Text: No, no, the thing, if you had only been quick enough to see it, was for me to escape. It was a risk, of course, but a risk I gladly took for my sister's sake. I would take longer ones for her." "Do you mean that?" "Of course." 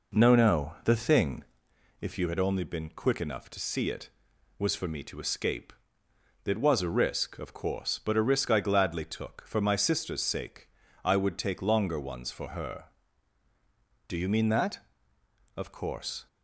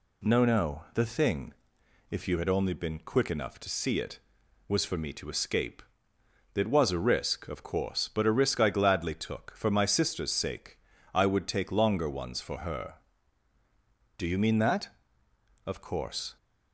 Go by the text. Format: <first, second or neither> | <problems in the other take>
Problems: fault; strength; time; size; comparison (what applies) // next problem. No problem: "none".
second | starts louder than the rest; noticeable; until 1.6 s; 4.5 dB